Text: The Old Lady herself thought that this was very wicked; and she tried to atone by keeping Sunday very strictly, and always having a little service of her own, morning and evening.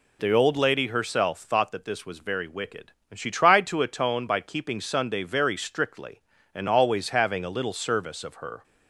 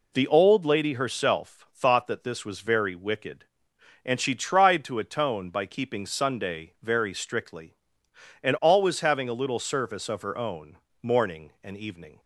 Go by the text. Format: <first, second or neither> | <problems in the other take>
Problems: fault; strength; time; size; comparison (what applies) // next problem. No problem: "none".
second | stops before "own morning and evening"; at 8.6 s